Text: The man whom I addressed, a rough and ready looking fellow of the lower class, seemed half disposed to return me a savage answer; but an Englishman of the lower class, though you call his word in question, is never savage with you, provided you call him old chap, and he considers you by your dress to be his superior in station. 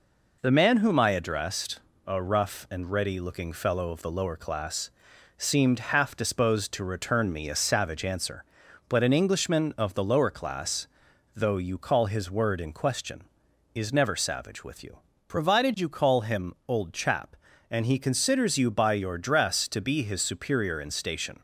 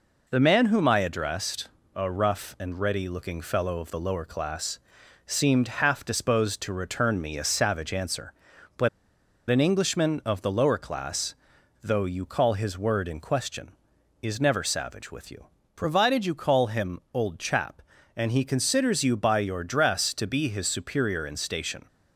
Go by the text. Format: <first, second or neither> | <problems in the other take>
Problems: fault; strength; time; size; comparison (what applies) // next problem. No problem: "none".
first | pauses between "but" and "an"; noticeable; at 8.8 s; 0.60 s long